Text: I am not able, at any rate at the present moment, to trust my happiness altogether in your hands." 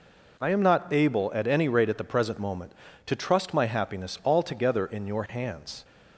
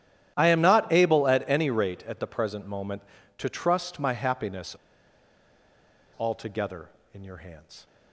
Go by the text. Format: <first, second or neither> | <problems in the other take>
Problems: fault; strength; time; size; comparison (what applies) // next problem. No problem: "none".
first | starts louder than the rest; strong; until 1.3 s; 11.5 dB // pauses between "happiness" and "altogether"; strong; at 4.7 s; 1.4 s long